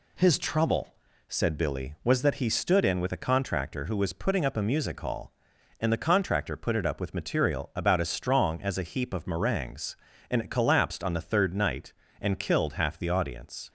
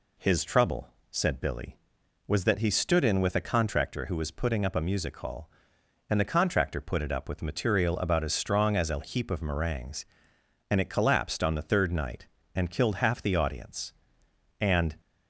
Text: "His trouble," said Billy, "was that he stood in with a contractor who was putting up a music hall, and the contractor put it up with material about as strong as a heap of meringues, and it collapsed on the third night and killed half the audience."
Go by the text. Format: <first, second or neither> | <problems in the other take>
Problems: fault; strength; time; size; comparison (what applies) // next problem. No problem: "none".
first | goes on to say "And"; slight; from 14.6 s on; 0.36 s long